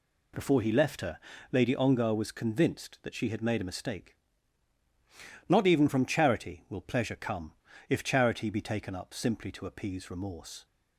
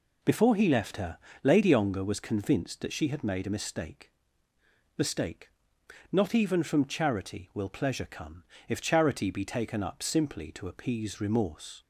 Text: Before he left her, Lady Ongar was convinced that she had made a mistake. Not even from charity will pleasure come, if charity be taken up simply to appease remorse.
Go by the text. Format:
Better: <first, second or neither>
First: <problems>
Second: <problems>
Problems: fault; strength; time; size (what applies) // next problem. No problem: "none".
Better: first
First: none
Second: says "mistake" twice; at 4.9 s